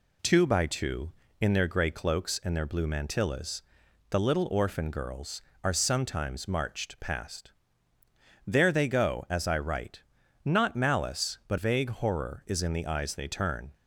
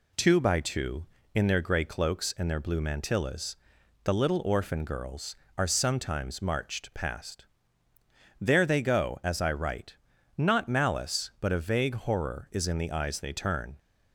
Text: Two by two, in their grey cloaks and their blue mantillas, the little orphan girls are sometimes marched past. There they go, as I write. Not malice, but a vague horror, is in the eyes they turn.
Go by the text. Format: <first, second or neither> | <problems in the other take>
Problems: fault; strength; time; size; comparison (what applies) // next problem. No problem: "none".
second | skips "a"; at 11.5 s